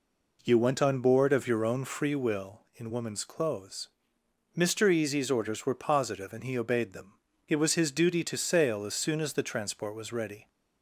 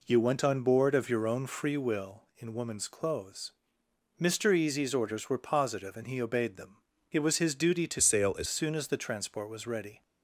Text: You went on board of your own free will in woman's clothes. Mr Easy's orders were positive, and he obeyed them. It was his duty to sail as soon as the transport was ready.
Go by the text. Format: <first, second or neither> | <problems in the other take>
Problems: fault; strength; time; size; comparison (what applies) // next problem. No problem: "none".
first | changes voice from "sail" to "as"; from 7.9 to 8.4 s; 0.5 s long